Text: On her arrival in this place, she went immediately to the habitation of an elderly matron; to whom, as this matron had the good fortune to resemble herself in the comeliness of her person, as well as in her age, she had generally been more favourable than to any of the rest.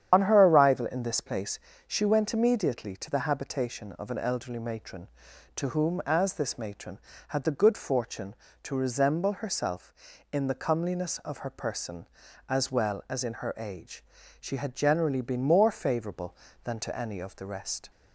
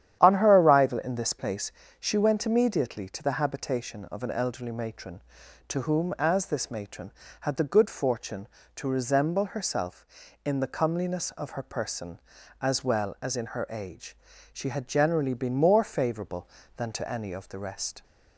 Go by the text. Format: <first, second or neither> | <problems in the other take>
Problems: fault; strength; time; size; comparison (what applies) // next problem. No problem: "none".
second | loses the start of "On"; at 0.1 s; 50 ms // starts louder than the rest; strong; until 1.1 s; 9.5 dB; strong in the second